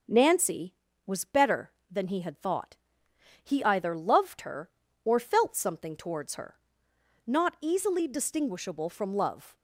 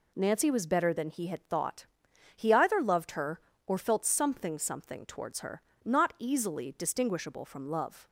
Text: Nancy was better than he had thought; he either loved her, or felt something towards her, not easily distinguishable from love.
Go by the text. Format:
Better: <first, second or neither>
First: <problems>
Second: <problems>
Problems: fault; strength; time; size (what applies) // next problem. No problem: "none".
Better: first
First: none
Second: says "something" twice; at 4.5 s